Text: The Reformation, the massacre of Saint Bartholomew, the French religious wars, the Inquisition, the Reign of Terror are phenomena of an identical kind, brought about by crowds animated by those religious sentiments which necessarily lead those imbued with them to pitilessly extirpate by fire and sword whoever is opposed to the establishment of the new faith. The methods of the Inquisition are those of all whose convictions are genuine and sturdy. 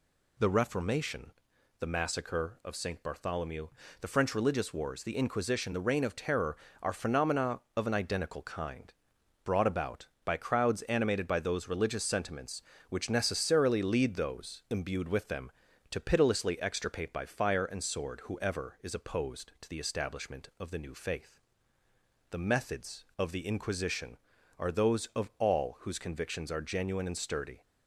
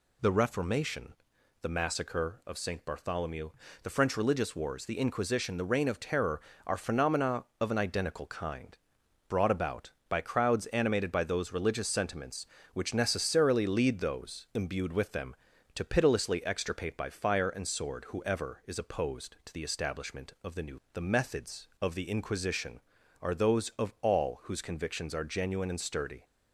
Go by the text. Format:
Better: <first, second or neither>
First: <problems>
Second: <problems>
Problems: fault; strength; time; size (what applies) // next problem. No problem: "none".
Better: first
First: none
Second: skips "faith"; at 20.8 s